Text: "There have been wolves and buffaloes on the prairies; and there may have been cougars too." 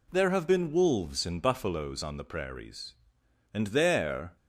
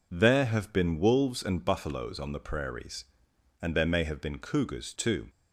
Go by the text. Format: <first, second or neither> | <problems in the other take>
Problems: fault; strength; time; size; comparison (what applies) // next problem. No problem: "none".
second | stops before "may have been cougars too"; at 4.3 s